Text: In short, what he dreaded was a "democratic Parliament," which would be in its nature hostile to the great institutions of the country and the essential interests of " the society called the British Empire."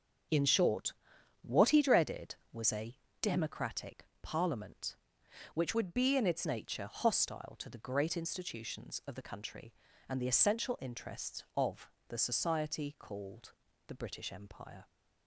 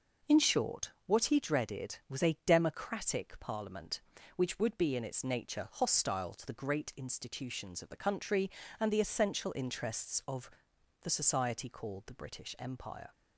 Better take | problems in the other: second | starts louder than the rest; until 1.7 s; 7 dB // pauses between "a" and "democratic"; slight; at 2.9 s; 0.28 s long // pauses between "democratic" and "Parliament"; slight; at 4.0 s; 0.16 s long // changes voice from "would" to "its"; from 5.7 to 6.4 s; 0.7 s long // pauses between "called" and "the"; slight; at 13.5 s; 0.36 s long

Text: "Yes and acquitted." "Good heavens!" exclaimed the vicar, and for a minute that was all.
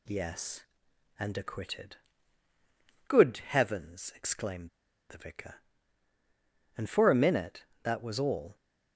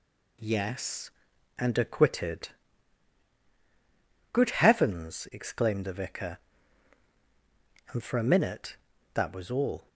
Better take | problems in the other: second | pauses between "exclaimed" and "the"; at 4.6 s; 0.39 s long

